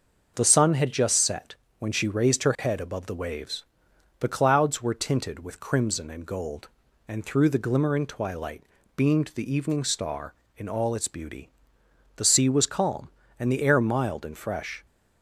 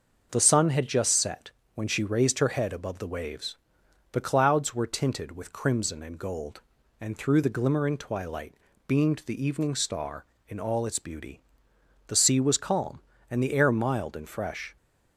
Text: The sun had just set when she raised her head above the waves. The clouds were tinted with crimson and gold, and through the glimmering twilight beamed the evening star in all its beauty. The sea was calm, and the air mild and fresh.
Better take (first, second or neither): neither